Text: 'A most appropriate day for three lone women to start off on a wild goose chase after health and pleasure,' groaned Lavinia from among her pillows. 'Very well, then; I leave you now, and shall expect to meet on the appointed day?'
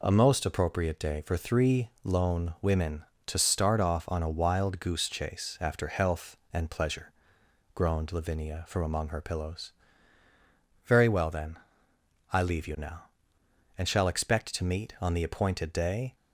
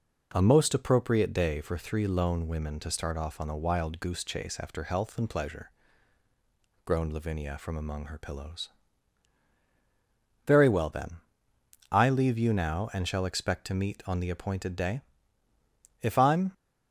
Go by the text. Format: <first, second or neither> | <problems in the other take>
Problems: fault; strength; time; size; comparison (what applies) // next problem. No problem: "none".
first | goes on to say "If I'm"; from 16.0 s on; 0.52 s long